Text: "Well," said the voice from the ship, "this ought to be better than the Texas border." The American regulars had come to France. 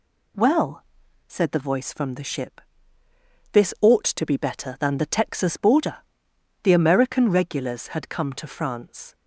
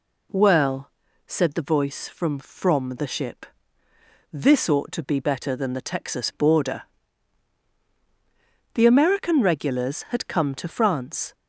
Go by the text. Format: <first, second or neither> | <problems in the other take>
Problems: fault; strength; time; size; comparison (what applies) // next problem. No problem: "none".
first | says "from" twice; at 2.3 s